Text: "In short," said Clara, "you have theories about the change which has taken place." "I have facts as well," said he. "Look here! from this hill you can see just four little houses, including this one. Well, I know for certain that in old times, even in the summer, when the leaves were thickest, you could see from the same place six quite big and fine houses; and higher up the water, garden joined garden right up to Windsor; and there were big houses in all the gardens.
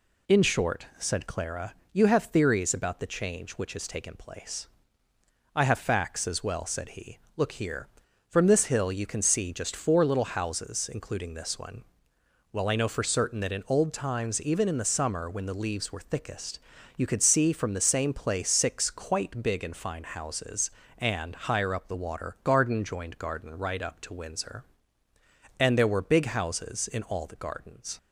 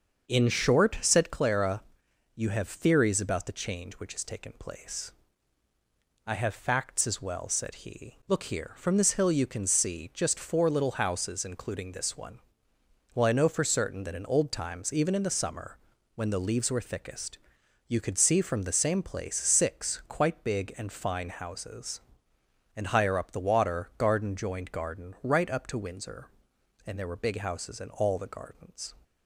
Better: first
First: none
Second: starts louder than the rest; until 1.4 s; 6.5 dB

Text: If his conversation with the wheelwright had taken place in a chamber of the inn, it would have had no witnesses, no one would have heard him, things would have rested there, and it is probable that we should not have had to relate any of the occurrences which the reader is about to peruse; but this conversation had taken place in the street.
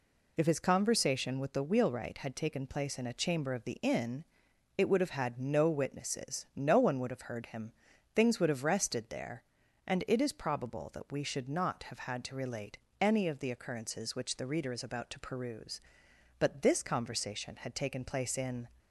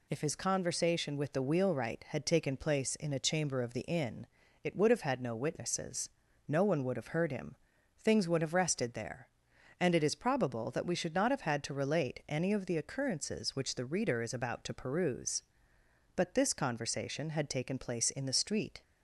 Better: second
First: pauses between "relate" and "any"; slight; at 12.7 s; 0.24 s long // stops before "the street"; at 18.7 s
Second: none

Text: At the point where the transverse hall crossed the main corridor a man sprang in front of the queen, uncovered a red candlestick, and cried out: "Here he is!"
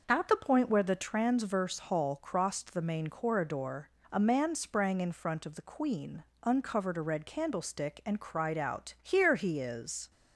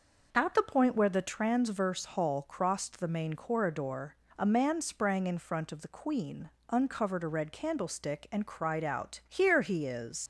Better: first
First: pauses between "corridor" and "a"; slight; at 3.8 s; 0.24 s long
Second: pauses between "corridor" and "a"; slight; at 4.1 s; 0.24 s long // leaves "is" unfinished; at 10.2 s; 100 ms

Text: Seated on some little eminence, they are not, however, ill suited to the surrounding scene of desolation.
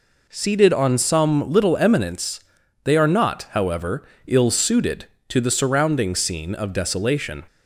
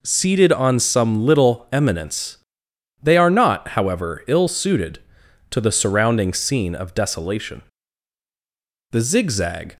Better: first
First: none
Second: goes on to say "The zigzag"; noticeable; from 8.9 s on; 0.84 s long

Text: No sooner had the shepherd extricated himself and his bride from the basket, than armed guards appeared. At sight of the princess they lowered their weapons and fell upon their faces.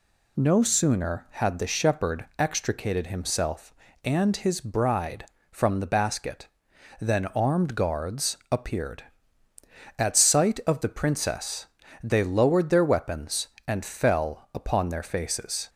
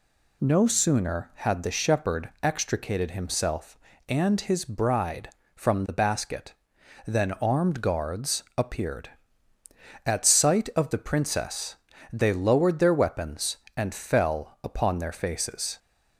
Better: neither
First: pauses between "guards" and "appeared"; slight; at 8.3 s; 0.16 s long // pauses between "princess" and "they"; slight; at 11.6 s; 0.36 s long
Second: pauses between "guards" and "appeared"; slight; at 8.4 s; 0.16 s long // pauses between "princess" and "they"; slight; at 11.7 s; 0.36 s long

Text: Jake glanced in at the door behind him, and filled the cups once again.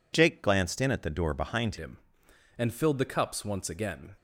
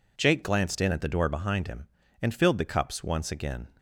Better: second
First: changes voice at "him"; from 1.7 s on; 2.4 s long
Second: none

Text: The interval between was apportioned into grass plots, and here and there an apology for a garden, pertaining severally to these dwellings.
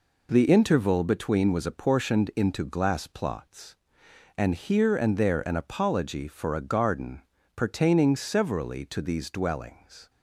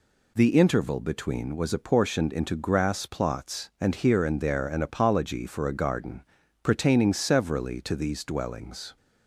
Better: second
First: says "glass" for "grass"; at 2.6 s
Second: none

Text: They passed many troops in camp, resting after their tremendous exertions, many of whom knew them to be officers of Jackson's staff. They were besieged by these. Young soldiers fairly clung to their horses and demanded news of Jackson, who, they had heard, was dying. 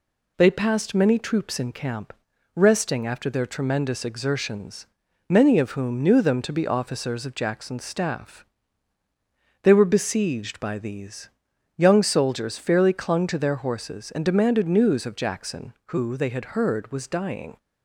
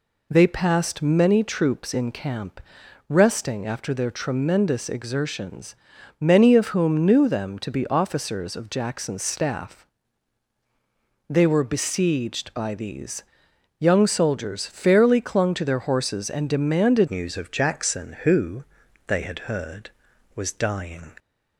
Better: first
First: none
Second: changes voice at "news"; from 17.0 s on; 4.1 s long

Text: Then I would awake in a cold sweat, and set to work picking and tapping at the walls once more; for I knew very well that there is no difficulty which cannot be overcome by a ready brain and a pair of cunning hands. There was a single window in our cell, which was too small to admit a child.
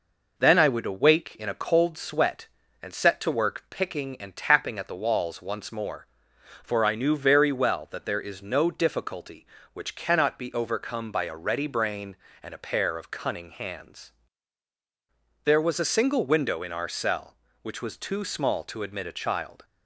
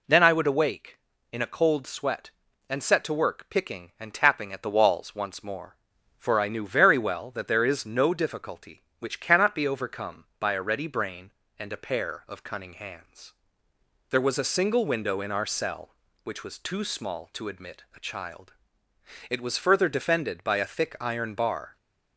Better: first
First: none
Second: goes on to say "It was further defended by a thick iron bar"; strong; from 19.3 s on; 2.4 s long

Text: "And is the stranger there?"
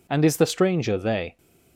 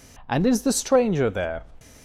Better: second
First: says "they" for "there"; at 0.9 s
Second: none

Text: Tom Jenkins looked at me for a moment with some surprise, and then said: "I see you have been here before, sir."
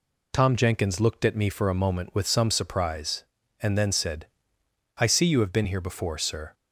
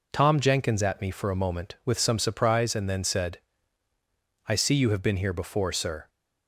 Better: first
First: none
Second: skips "looked"; at 0.8 s

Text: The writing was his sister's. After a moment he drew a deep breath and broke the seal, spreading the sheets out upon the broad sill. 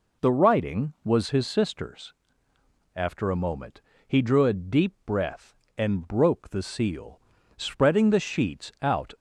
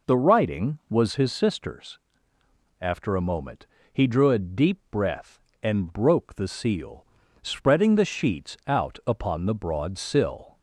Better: second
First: pauses between "moment" and "he"; slight; at 3.8 s; 0.24 s long // stops before "upon the broad sill"; at 9.1 s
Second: pauses between "moment" and "he"; slight; at 3.6 s; 0.24 s long

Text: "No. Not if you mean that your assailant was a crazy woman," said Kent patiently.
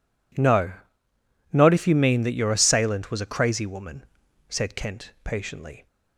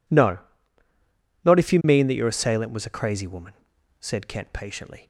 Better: neither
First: none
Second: none

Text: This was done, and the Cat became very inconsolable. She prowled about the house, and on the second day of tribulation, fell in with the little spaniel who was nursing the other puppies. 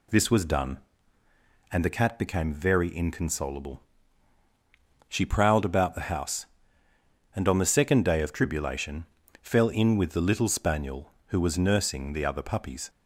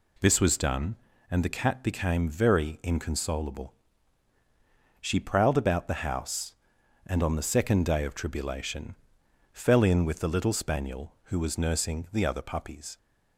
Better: neither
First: none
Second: none

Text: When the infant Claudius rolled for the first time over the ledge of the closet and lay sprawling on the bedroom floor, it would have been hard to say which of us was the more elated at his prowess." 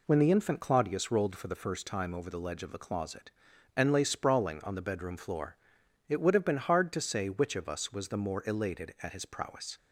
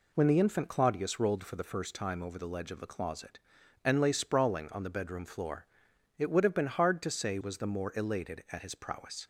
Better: first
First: none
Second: skips "which of us"; at 7.4 s

